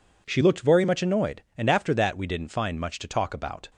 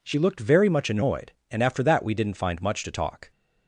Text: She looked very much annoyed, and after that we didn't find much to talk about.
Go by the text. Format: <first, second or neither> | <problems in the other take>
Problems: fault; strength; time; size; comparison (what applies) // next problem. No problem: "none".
first | stops before "about"; at 3.3 s